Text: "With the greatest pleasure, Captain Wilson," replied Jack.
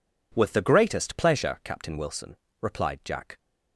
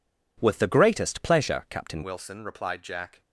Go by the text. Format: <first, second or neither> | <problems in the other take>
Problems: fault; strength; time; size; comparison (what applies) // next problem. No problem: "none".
first | changes voice at "Wilson"; from 2.0 s on; 1.2 s long